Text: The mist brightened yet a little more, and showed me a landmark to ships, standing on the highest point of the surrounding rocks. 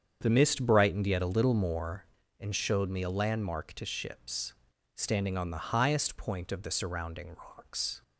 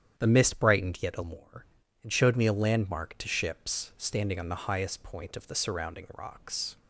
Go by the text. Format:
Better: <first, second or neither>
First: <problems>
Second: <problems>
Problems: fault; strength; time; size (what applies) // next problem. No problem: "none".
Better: first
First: starts louder than the rest; strong; until 1.2 s; 7.5 dB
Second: starts louder than the rest; strong; until 1.1 s; 9 dB // skips "little"; at 1.2 s